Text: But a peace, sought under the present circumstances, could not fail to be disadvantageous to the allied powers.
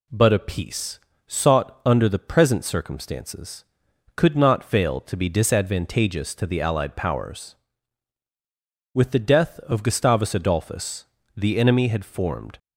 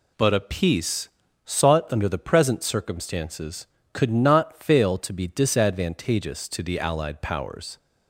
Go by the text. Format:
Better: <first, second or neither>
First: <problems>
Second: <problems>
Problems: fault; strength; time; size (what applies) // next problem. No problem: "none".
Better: second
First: goes on to say "With the death of Gustavus Adolphus the enemy had formed"; strong; from 8.9 s on; 3.6 s long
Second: none